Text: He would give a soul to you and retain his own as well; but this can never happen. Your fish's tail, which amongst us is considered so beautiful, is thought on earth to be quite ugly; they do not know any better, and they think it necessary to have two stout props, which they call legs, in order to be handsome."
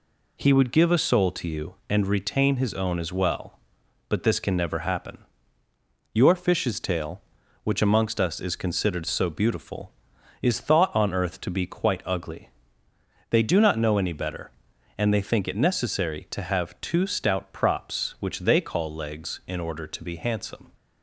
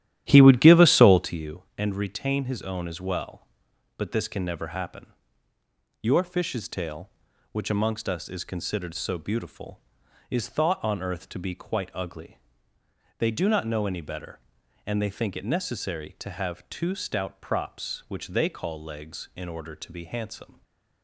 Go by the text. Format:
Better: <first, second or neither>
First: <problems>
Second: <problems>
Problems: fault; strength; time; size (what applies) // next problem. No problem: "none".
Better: first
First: none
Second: starts louder than the rest; strong; until 1.4 s; 12 dB // stays silent after the last word; slight; from 20.5 s on; 0.5 s long